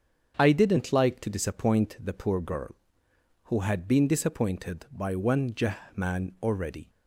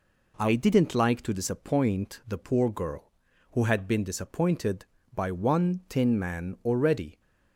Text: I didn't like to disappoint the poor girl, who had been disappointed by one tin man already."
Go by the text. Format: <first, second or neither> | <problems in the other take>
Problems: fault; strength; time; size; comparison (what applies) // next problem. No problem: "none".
second | starts louder than the rest; until 1.3 s; 7 dB // says "jah" for "tin"; at 5.5 s